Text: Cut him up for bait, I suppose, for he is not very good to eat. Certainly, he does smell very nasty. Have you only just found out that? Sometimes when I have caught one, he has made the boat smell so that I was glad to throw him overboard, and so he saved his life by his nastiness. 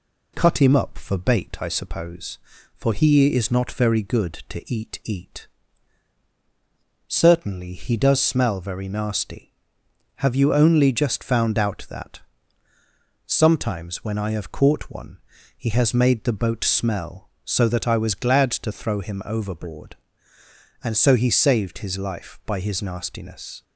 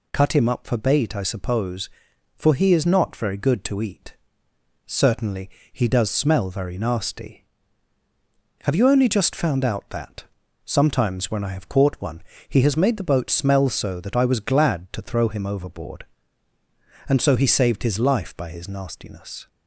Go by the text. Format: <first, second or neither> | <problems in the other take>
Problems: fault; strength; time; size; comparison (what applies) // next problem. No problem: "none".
second | says "eat" twice; at 5.0 s